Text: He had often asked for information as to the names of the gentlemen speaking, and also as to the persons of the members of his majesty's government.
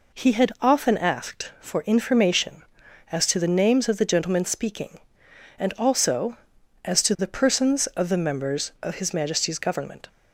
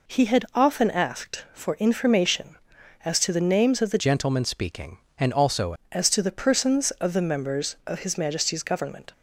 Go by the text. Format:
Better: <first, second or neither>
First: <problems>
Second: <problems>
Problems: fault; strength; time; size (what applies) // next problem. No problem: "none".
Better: first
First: none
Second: changes voice from "gentlemen" to "also"; from 3.9 to 5.7 s; 1.8 s long